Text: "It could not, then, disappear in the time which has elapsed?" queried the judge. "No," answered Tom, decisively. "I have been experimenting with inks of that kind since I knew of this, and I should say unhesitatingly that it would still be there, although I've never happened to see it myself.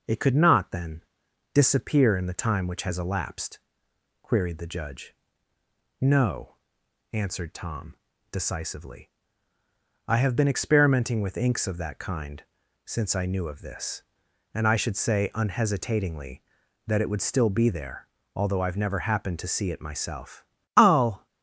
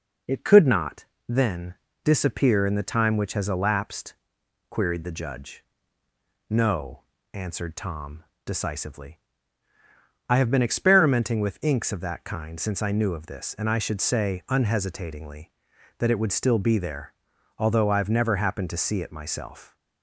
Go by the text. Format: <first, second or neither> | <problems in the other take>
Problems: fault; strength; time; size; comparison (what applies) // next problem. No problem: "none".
second | pauses between "kind" and "since"; at 12.4 s; 0.42 s long // goes on to say "I'll"; from 20.7 s on; 0.50 s long